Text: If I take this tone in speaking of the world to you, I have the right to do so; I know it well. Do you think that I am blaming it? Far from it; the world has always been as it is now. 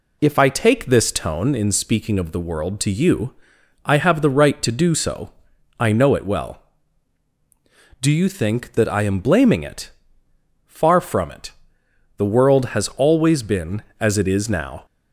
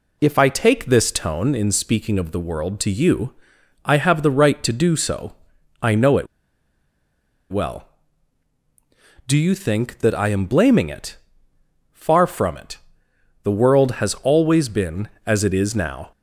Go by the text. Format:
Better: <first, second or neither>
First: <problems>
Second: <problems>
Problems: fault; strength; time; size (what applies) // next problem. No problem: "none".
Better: first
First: none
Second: pauses between "it" and "well"; at 6.2 s; 1.2 s long